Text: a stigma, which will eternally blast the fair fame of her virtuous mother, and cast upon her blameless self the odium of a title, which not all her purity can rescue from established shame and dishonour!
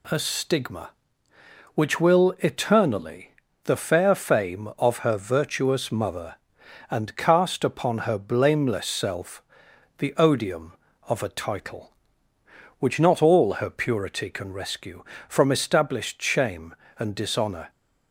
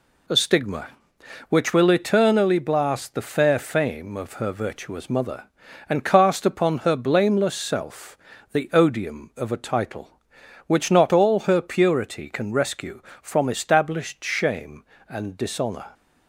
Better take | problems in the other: second | skips "blast"; at 3.4 s // pauses between "self" and "the"; noticeable; at 9.4 s; 0.56 s long; slight in the second

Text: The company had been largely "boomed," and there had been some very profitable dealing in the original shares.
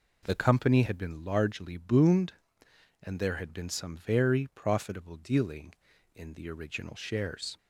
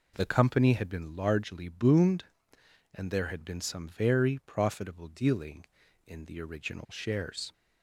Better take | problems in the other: neither | none

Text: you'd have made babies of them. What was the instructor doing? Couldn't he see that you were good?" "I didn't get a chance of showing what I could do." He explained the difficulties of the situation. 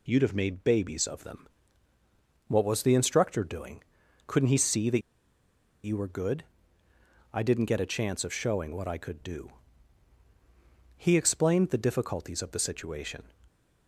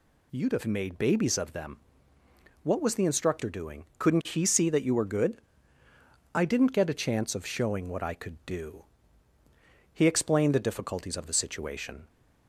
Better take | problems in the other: second | pauses between "that" and "you"; noticeable; at 5.0 s; 0.83 s long

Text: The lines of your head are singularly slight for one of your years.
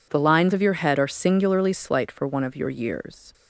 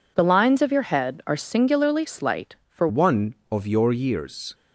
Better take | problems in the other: first | changes voice at "one"; from 2.8 s on; 1.7 s long

